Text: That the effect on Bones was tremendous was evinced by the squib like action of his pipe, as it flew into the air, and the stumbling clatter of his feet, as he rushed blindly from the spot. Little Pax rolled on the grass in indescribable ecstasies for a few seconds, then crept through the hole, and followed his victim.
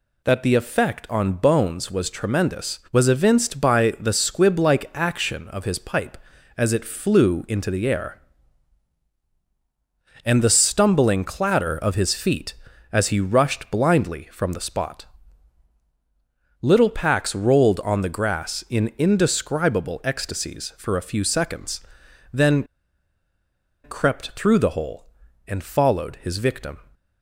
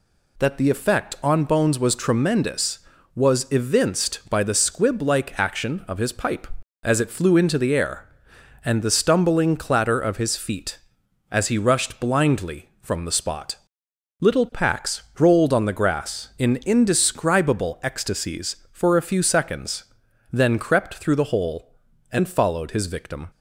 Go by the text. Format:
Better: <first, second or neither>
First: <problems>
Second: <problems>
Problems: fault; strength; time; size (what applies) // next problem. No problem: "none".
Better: second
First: pauses between "then" and "crept"; at 22.6 s; 1.2 s long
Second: none